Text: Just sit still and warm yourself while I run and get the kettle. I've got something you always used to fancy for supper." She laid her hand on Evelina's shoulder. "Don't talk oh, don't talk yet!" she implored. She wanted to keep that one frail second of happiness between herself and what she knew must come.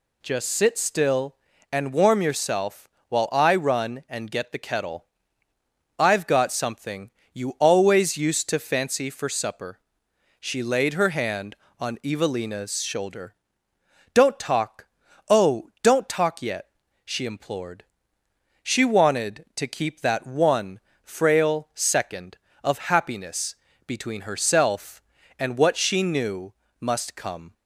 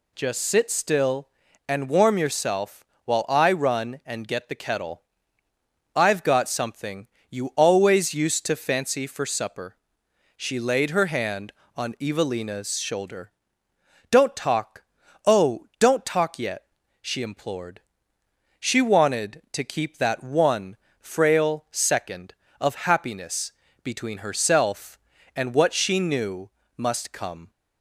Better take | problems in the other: neither | pauses between "yourself" and "while"; slight; the same in both // pauses between "something" and "you"; slight; the same in both // pauses between "talk" and "oh"; noticeable; the same in both // pauses between "one" and "frail"; slight; the same in both // pauses between "happiness" and "between"; slight; the same in both // pauses between "knew" and "must"; slight; the same in both

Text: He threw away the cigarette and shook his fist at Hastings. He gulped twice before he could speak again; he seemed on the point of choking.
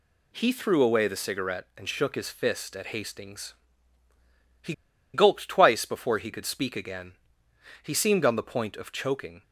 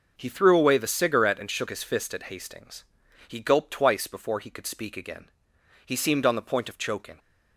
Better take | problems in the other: second | pauses between "He" and "gulped"; at 4.7 s; 0.40 s long

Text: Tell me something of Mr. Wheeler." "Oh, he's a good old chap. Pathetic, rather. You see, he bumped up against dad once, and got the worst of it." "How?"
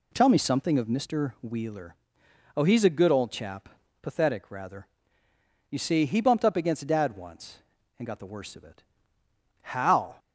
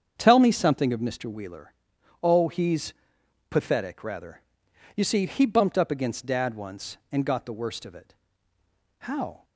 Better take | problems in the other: first | starts louder than the rest; strong; until 1.2 s; 7.5 dB // skips "a good old chap"; at 3.2 s

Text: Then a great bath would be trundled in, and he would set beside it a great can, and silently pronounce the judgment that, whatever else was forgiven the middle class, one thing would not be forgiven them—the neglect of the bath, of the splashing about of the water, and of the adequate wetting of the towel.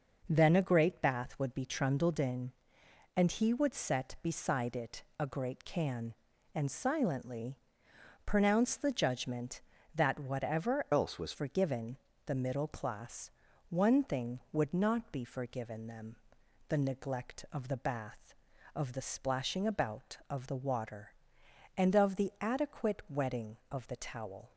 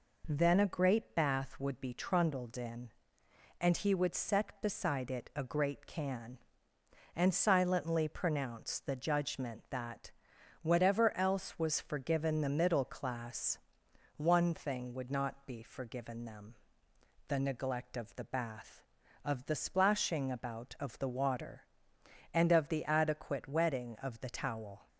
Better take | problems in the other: second | pauses between "it" and "a"; slight; at 5.0 s; 0.16 s long // pauses between "silently" and "pronounce"; noticeable; at 7.5 s; 0.68 s long // changes voice from "else" to "was"; from 10.9 to 11.3 s; 0.4 s long // pauses between "forgiven" and "the"; slight; at 11.9 s; 0.30 s long

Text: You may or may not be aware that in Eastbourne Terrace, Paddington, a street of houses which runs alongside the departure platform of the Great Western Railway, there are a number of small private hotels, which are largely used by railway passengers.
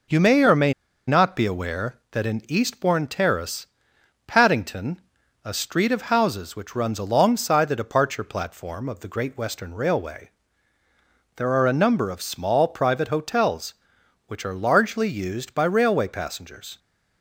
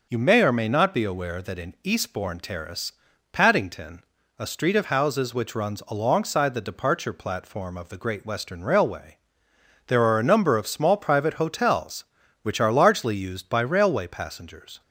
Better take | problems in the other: second | pauses between "may" and "not"; slight; at 0.7 s; 0.35 s long

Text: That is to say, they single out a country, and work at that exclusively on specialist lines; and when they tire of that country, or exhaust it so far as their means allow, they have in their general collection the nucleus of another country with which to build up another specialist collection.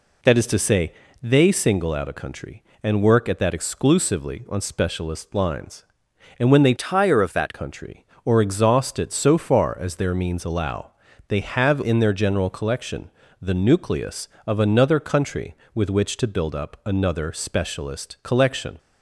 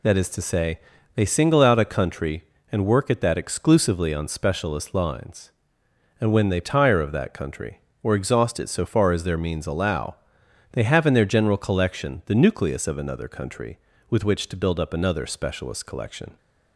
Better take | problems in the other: second | changes voice from "tire" to "that"; from 6.7 to 7.5 s; 0.8 s long // pauses between "collection" and "the"; slight; at 13.0 s; 0.32 s long

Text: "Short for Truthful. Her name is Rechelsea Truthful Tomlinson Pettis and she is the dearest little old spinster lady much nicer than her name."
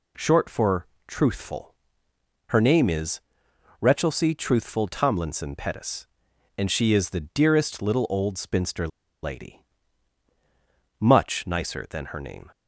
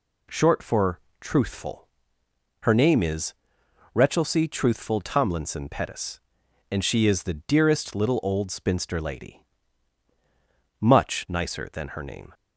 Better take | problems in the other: second | pauses between "for" and "Truthful"; slight; at 0.8 s; 0.20 s long; slight in the second // pauses between "is" and "Rechelsea"; noticeable; at 3.1 s; 0.62 s long; noticeable in the second // pauses between "spinster" and "lady"; slight; at 8.8 s; 0.35 s long // pauses between "lady" and "much"; strong; at 9.6 s; 1.4 s long; strong in the second

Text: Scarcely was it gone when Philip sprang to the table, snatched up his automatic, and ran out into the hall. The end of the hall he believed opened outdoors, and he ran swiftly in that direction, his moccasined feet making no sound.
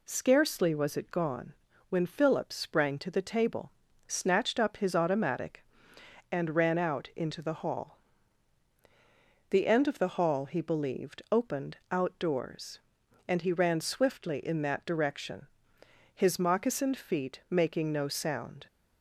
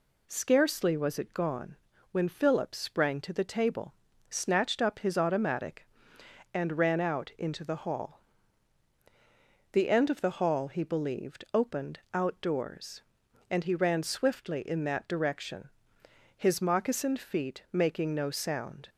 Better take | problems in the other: neither | pauses between "gone" and "when"; slight; the same in both

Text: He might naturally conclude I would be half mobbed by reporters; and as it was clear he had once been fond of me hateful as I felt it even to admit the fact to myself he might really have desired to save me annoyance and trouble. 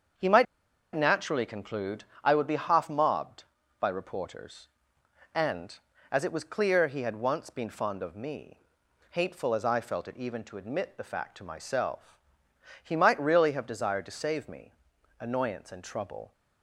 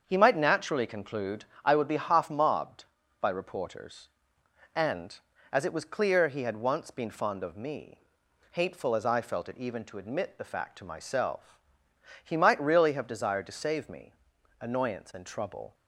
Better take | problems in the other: second | starts louder than the rest; until 1.6 s; 7 dB; also in the second // pauses between "might" and "naturally"; noticeable; at 0.4 s; 0.50 s long // pauses between "conclude" and "I"; slight; at 2.0 s; 0.20 s long; slight in the second // pauses between "me" and "hateful"; noticeable; at 8.5 s; 0.52 s long; noticeable in the second // pauses between "myself" and "he"; noticeable; at 12.1 s; 0.64 s long; noticeable in the second // pauses between "me" and "annoyance"; noticeable; at 14.7 s; 0.48 s long; noticeable in the second

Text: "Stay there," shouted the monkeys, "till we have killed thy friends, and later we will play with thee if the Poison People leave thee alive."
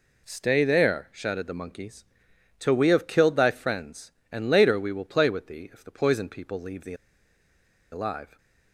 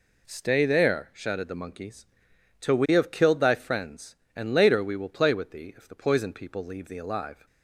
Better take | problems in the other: second | pauses between "thee" and "alive"; at 6.9 s; 0.98 s long

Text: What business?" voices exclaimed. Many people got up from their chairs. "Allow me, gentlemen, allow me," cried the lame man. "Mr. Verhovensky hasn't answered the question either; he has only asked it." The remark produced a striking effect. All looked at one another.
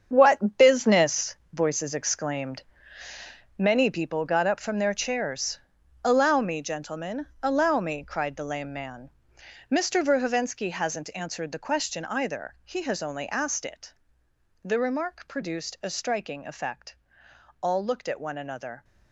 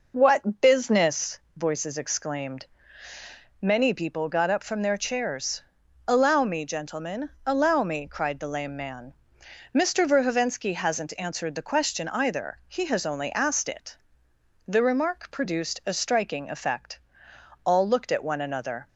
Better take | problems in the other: second | gets quieter; strong; throughout; 10.5 dB

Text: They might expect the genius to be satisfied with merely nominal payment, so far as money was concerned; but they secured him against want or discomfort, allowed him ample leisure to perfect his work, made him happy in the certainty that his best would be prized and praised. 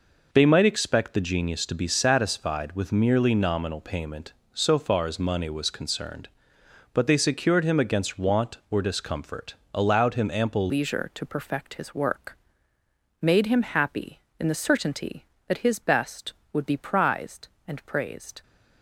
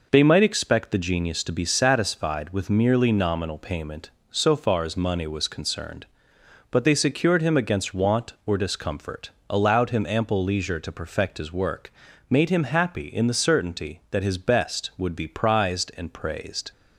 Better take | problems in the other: second | changes voice at "leisure"; from 10.6 s on; 7.8 s long

